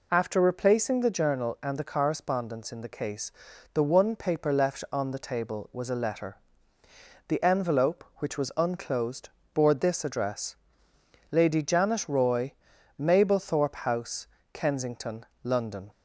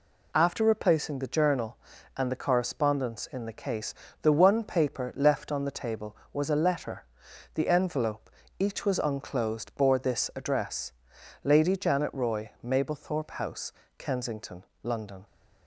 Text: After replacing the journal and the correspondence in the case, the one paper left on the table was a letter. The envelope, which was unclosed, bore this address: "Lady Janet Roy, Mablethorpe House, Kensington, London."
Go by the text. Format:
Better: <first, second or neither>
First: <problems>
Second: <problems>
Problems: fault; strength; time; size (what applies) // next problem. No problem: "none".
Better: first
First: none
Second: says "each" for "which"; at 8.5 s